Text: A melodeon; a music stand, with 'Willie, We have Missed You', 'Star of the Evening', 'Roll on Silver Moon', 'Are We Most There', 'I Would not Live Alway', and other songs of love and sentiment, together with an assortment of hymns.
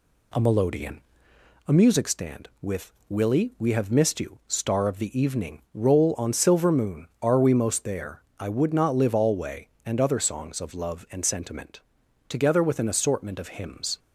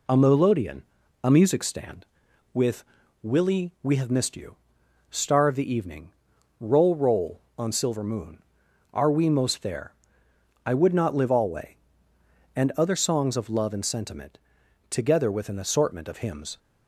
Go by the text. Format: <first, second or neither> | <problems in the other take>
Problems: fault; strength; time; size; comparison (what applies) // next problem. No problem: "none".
first | pauses between "with" and "Willie"; at 2.8 s; 0.40 s long; slight in the first // says "Roll" twice; at 6.9 s